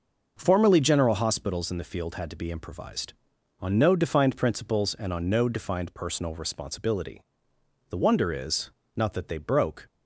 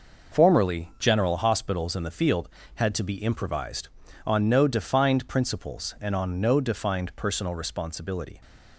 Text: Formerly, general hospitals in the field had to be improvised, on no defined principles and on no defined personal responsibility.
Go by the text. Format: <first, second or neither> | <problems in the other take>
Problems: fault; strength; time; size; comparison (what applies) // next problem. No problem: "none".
second | goes on to say "The wonder is not that they broke"; strong; from 7.8 s on; 1.9 s long